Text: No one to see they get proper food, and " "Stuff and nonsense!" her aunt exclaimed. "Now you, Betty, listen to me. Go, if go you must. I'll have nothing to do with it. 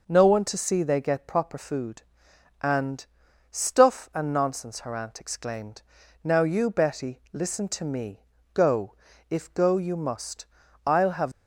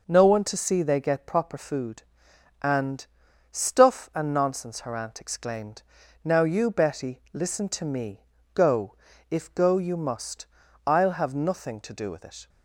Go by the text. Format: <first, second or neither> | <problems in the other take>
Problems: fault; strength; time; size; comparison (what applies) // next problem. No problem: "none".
second | stops before "nothing to do with it"; at 11.3 s